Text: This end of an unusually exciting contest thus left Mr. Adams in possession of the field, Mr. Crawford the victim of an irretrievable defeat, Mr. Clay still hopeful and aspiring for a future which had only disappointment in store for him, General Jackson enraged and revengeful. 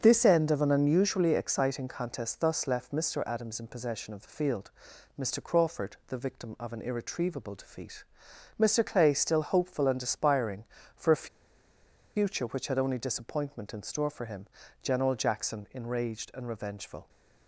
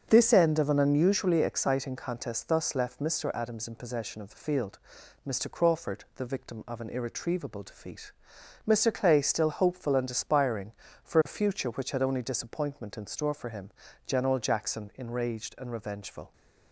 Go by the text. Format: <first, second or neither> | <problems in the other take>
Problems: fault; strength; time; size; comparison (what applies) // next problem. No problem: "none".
second | starts louder than the rest; until 1.0 s; 7 dB; also in the second // pauses between "a" and "future"; noticeable; at 11.2 s; 0.88 s long